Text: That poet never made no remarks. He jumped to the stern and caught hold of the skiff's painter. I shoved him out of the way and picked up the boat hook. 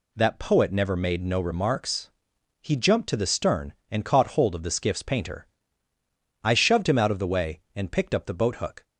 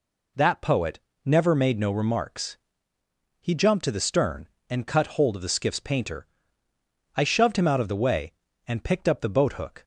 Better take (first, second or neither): first